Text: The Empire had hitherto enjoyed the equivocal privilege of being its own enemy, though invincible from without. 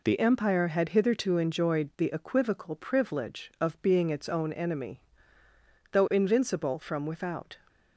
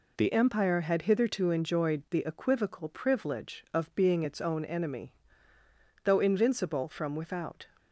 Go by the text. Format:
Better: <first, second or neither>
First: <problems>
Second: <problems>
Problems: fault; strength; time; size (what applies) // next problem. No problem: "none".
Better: neither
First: none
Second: none